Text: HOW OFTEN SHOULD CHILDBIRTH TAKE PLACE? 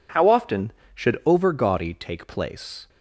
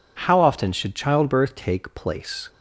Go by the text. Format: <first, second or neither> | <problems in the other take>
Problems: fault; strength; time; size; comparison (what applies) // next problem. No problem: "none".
second | says "Overgaudy" for "CHILDBIRTH"; at 1.2 s